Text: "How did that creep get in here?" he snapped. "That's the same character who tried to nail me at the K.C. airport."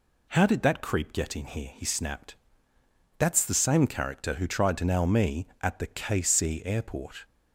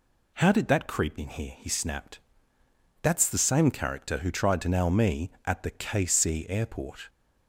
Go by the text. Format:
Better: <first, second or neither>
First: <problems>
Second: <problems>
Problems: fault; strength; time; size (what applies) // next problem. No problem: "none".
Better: first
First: none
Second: skips "get"; at 1.1 s